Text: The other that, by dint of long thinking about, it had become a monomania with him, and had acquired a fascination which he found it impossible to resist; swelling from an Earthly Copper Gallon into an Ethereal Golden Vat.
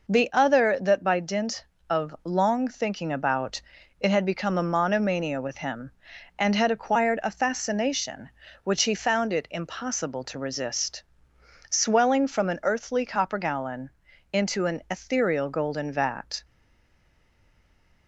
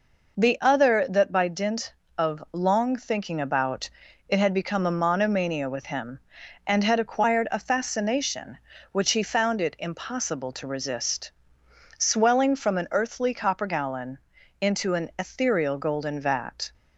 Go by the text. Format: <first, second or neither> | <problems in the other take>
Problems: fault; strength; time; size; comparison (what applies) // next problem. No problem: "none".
second | pauses between "Gallon" and "into"; at 13.9 s; 0.42 s long; also in the second // stays silent after the last word; noticeable; from 16.4 s on; 1.6 s long